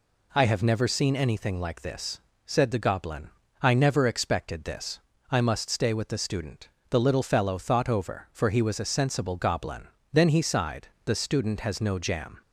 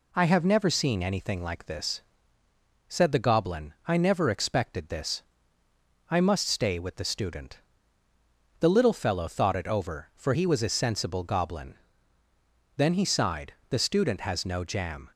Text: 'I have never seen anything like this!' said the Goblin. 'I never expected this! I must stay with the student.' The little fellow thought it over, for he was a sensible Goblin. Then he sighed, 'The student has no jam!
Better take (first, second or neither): second